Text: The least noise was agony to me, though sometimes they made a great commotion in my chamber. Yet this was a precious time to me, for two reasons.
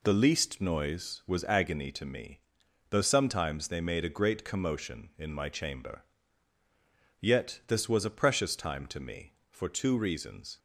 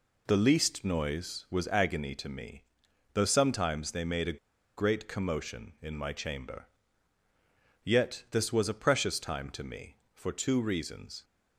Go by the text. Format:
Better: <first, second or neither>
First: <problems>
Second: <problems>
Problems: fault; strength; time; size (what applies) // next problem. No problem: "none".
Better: first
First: none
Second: pauses between "a" and "great"; at 4.3 s; 0.41 s long